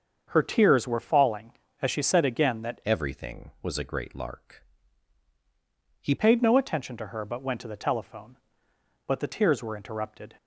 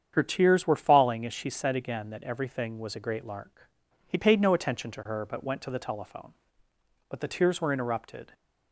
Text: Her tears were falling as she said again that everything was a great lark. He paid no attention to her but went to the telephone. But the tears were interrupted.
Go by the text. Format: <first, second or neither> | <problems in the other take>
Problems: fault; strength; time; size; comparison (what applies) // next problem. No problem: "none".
second | starts louder than the rest; until 1.2 s; 7 dB; strong in the second // changes voice from "everything" to "He"; from 2.8 to 6.1 s; 3.3 s long